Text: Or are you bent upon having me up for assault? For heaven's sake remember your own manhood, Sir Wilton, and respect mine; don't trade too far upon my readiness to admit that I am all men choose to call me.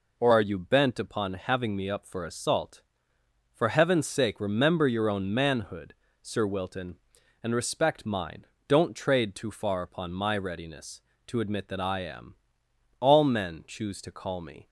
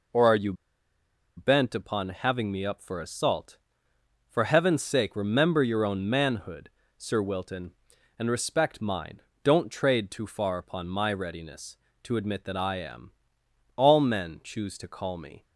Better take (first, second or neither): first